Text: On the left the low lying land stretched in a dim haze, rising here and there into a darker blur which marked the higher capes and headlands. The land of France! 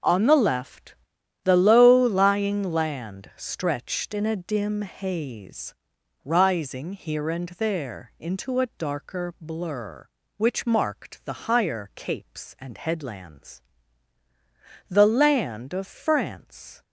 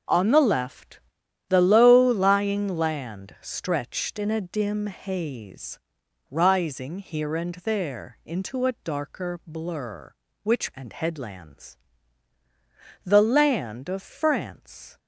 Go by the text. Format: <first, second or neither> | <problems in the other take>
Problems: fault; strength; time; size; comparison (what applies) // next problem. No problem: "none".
first | pauses between "left" and "the"; noticeable; at 0.9 s; 0.48 s long; noticeable in the first // skips "marked the higher capes"; at 10.7 s